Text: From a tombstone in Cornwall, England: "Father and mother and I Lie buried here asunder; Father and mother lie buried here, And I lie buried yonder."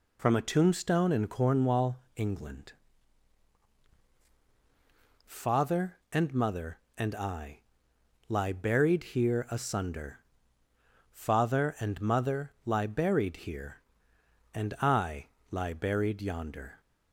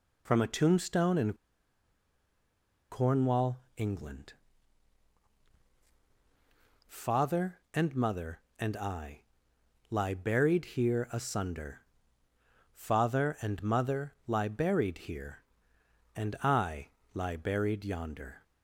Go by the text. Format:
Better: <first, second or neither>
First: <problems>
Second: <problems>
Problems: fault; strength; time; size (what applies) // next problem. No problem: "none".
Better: first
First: pauses between "I" and "Lie"; noticeable; at 7.6 s; 0.66 s long // pauses between "I" and "lie"; slight; at 15.2 s; 0.24 s long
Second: pauses between "in" and "Cornwall"; strong; at 1.3 s; 1.5 s long // pauses between "I" and "Lie"; noticeable; at 9.2 s; 0.66 s long // pauses between "I" and "lie"; slight; at 16.8 s; 0.26 s long